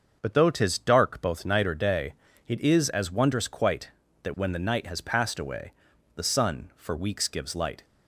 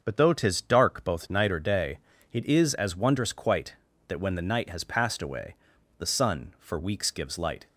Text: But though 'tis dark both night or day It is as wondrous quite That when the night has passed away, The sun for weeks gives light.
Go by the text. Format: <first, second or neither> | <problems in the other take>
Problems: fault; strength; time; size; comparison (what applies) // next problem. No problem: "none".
neither | starts louder than the rest; the same in both // pauses between "day" and "It"; slight; the same in both